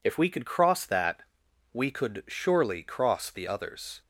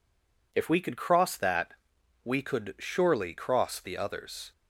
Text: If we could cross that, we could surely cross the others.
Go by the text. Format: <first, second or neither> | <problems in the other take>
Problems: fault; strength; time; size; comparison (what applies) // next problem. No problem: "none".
first | stays silent before the first word; slight; until 0.5 s; 0.5 s long